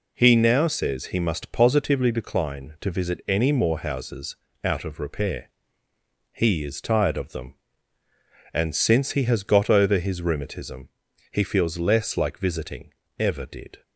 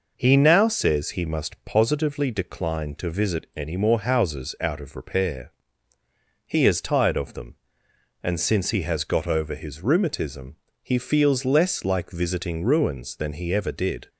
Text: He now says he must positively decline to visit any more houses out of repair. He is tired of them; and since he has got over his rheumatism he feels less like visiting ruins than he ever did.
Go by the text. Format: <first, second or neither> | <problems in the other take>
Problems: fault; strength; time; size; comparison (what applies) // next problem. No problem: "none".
second | pauses between "houses" and "out"; slight; at 4.3 s; 0.26 s long // pauses between "rheumatism" and "he"; at 10.8 s; 0.42 s long; slight in the second // skips "ruins than he"; at 13.0 s